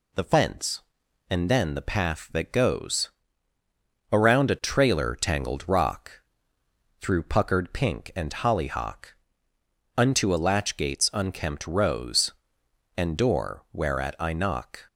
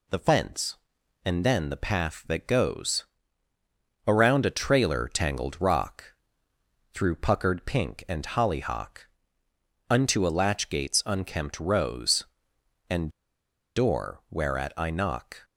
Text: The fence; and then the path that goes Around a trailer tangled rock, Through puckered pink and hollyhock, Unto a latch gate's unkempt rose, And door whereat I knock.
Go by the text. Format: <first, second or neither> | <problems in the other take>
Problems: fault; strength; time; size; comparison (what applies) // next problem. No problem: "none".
first | pauses between "goes" and "Around"; at 3.0 s; 1.0 s long; also in the first // pauses between "And" and "door"; noticeable; at 13.0 s; 0.66 s long